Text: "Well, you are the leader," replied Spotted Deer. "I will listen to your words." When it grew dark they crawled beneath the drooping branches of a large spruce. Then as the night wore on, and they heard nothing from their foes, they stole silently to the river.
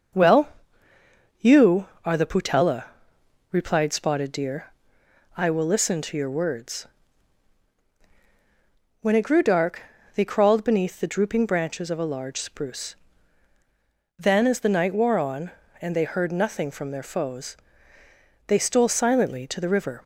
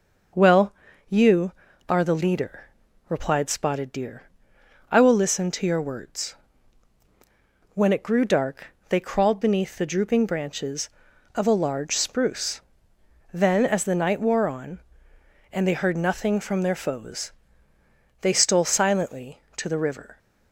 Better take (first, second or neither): second